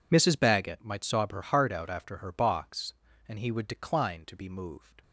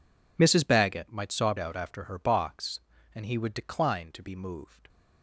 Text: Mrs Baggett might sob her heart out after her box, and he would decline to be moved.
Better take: first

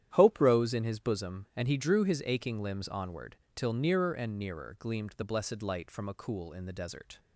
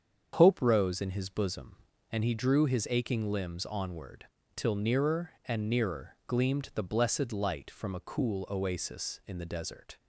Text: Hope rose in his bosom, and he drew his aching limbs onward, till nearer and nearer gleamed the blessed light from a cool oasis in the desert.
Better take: second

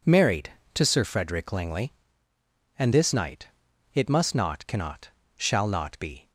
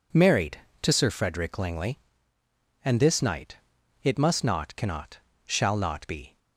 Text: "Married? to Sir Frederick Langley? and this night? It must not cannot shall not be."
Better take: neither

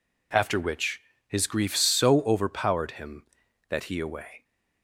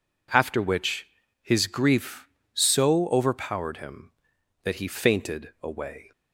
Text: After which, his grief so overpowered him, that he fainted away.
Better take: second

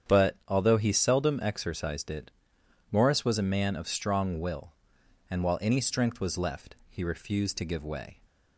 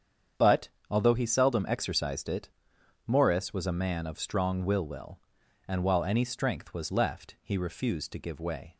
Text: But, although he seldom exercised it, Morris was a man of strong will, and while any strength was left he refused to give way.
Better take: first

